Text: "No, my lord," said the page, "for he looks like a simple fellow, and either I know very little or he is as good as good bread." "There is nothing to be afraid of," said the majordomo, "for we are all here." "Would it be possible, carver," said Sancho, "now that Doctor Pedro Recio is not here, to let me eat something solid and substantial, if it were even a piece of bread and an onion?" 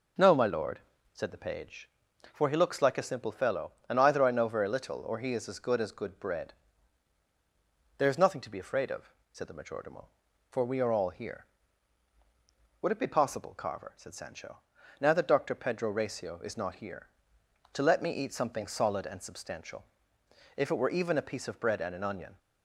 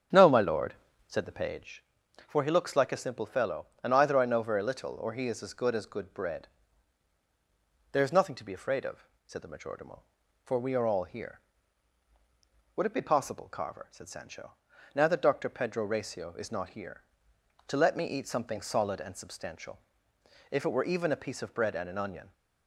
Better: first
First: none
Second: starts louder than the rest; strong; until 1.7 s; 8 dB

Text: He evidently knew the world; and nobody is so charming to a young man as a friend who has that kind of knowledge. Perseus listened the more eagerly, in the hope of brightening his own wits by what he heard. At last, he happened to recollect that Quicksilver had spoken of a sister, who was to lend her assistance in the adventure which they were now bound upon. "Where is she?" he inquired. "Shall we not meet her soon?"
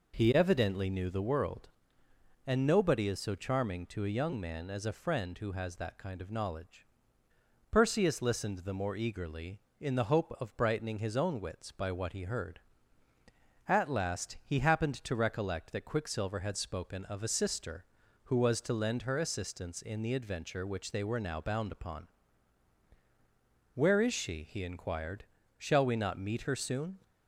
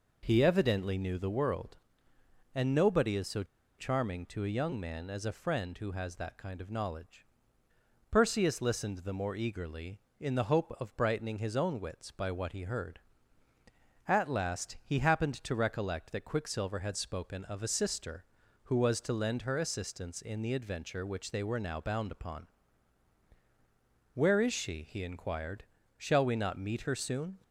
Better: first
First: none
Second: pauses between "so" and "charming"; slight; at 3.4 s; 0.34 s long

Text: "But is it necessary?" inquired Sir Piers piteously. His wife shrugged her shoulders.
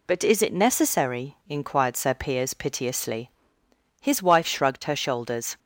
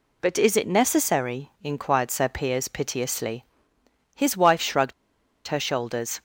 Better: first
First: none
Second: pauses between "shrugged" and "her"; noticeable; at 4.9 s; 0.55 s long

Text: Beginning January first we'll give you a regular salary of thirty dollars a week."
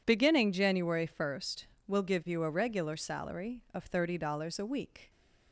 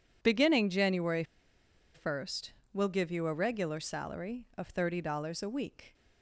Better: first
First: pauses between "first" and "we'll"; slight; at 1.6 s; 0.22 s long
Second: pauses between "January" and "first"; noticeable; at 1.2 s; 0.71 s long // pauses between "first" and "we'll"; slight; at 2.5 s; 0.22 s long

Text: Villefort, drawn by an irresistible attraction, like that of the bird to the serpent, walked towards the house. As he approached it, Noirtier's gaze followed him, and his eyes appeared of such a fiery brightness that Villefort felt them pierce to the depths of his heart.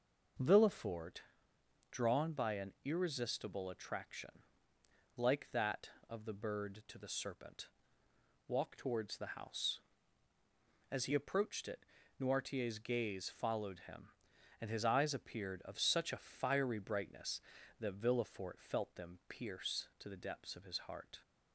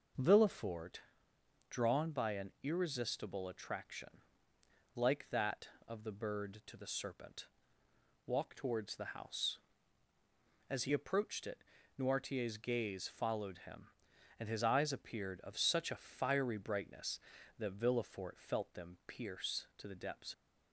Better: first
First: none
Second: stops before "of his heart"; at 20.3 s

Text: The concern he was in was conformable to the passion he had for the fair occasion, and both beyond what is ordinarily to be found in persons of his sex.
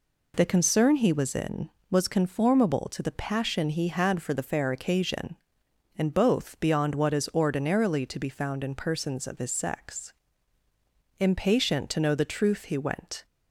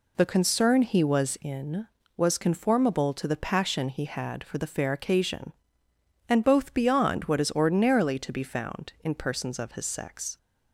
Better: second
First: goes on to say "Impatient to know the truth he went"; strong; from 11.1 s on; 2.0 s long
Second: none

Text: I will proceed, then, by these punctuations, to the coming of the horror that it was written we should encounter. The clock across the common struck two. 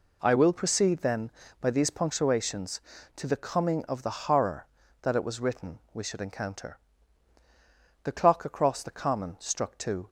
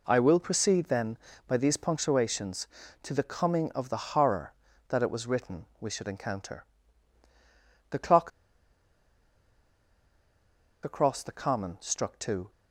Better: first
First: none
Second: pauses between "clock" and "across"; strong; at 8.3 s; 2.5 s long

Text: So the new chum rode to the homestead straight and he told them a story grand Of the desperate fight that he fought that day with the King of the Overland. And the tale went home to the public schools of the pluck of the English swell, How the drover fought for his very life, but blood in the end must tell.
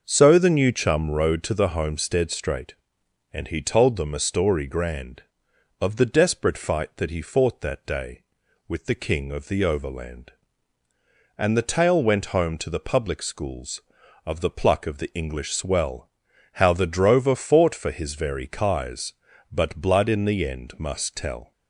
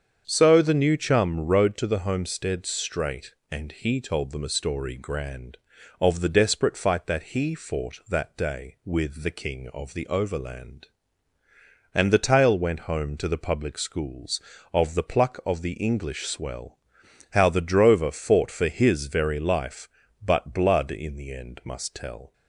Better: second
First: starts louder than the rest; noticeable; until 1.0 s; 6 dB // says "kies" for "life"; at 18.4 s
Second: starts louder than the rest; strong; until 1.2 s; 7.5 dB

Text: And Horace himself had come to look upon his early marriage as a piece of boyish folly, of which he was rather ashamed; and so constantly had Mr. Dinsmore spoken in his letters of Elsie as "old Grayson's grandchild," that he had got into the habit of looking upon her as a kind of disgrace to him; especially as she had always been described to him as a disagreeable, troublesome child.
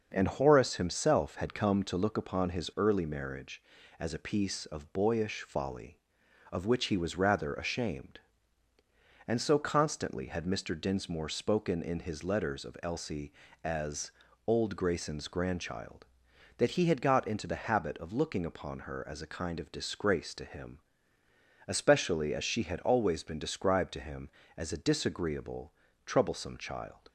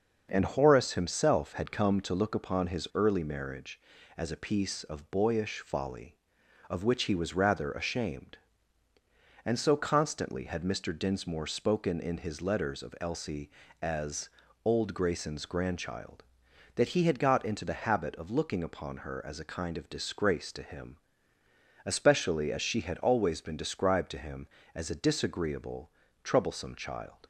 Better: neither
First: starts louder than the rest; until 1.1 s; 6.5 dB // pauses between "as" and "old"; slight; at 14.1 s; 0.34 s long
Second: starts louder than the rest; until 1.3 s; 6.5 dB // pauses between "as" and "old"; slight; at 14.3 s; 0.34 s long

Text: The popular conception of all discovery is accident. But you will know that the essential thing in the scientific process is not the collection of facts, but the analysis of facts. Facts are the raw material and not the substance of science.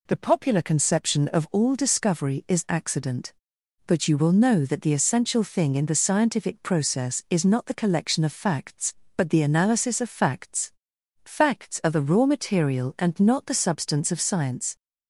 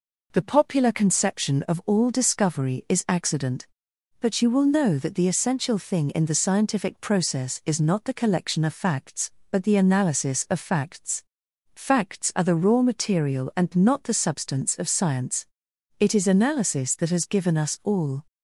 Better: first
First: none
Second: goes on to say "It is analysis that has given us all"; strong; from 15.9 s on; 2.2 s long

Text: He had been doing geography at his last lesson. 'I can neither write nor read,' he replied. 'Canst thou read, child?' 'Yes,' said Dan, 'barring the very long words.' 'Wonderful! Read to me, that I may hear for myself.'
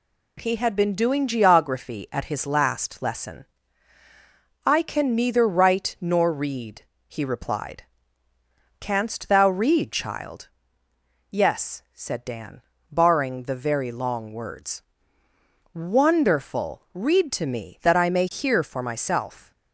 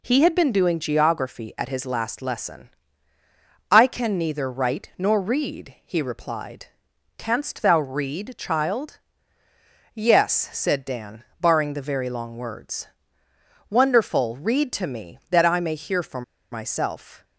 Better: first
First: none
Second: pauses between "for" and "myself"; slight; at 16.2 s; 0.29 s long

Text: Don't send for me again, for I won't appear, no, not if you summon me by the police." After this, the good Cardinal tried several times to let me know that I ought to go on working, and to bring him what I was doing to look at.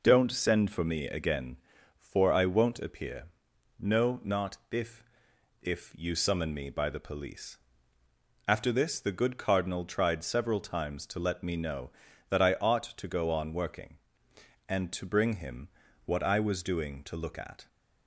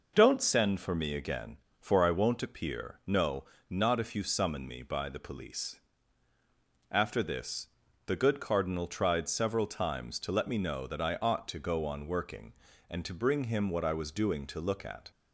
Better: second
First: says "if" twice; at 5.6 s // pauses between "him" and "what"; at 15.6 s; 0.38 s long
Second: none

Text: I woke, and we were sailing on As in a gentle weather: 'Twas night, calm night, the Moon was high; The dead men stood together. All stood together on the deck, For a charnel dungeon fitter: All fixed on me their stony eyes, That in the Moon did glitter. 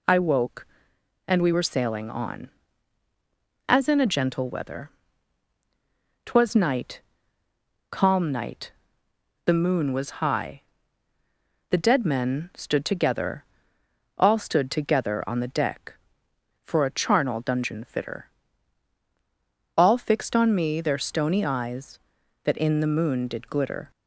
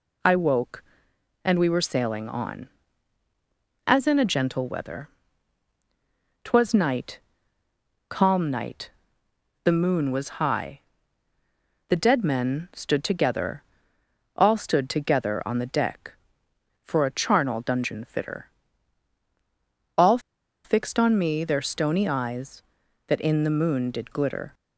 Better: first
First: none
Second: pauses between "All" and "fixed"; noticeable; at 20.1 s; 0.46 s long

